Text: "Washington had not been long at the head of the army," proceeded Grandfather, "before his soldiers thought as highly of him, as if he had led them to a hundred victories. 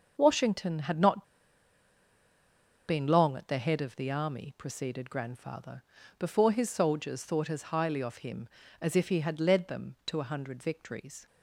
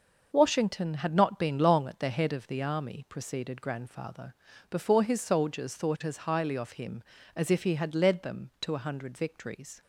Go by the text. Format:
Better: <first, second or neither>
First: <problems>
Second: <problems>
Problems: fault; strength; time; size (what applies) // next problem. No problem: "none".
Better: second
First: starts louder than the rest; until 1.1 s; 6 dB // pauses between "not" and "been"; strong; at 1.2 s; 1.6 s long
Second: starts louder than the rest; noticeable; until 1.3 s; 6 dB